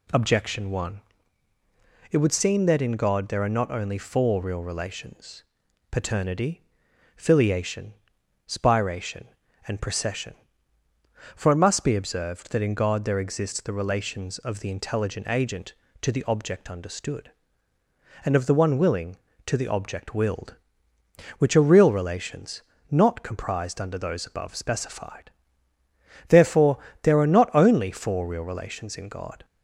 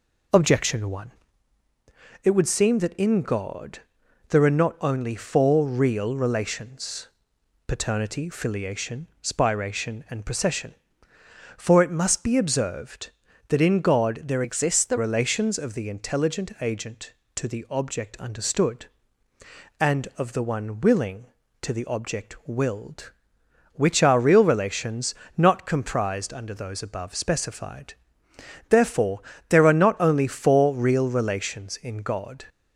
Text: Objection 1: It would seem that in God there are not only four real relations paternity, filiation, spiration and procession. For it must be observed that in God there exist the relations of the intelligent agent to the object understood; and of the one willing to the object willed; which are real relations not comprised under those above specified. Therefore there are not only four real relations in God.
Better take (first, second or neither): first